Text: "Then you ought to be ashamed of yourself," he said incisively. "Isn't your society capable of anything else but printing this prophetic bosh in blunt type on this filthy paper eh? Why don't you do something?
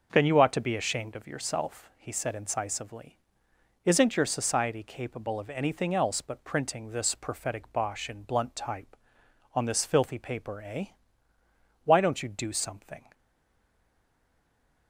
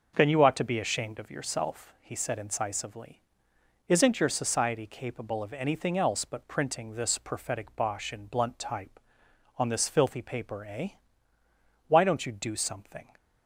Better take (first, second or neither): second